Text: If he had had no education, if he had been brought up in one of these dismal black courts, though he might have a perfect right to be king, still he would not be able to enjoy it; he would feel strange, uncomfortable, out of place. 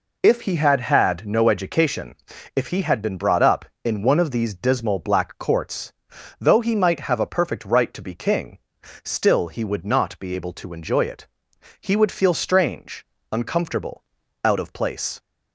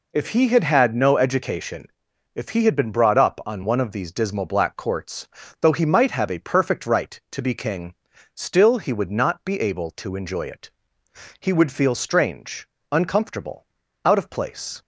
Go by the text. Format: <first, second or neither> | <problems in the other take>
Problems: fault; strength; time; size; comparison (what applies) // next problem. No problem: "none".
first | says "on" for "in"; at 3.4 s